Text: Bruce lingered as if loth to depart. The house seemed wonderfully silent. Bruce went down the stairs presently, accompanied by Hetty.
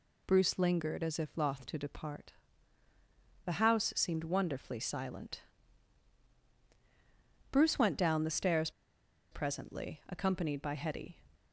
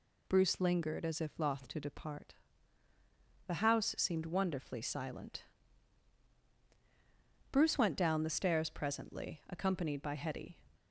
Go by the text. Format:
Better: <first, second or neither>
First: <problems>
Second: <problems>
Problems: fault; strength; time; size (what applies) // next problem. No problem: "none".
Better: second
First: pauses between "stairs" and "presently"; noticeable; at 8.7 s; 0.61 s long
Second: none